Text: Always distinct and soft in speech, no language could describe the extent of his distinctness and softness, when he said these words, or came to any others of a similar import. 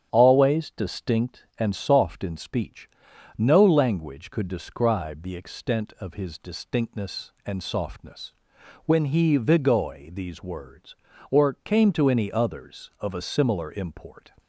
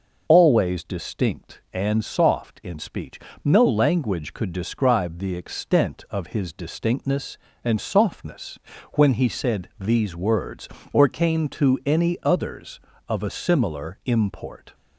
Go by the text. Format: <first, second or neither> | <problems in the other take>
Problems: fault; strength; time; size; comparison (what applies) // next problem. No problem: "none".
second | starts louder than the rest; strong; until 1.1 s; 9 dB // says "vigoi" for "said"; at 9.3 s